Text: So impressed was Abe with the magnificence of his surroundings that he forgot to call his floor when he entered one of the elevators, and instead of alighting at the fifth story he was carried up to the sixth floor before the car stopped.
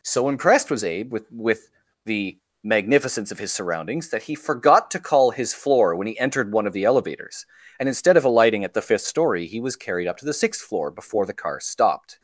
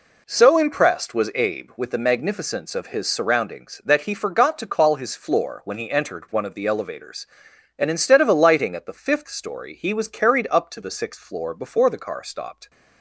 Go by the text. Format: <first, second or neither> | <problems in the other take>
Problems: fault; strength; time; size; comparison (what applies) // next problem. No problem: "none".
second | says "with" twice; at 1.3 s // pauses between "the" and "magnificence"; slight; at 2.3 s; 0.24 s long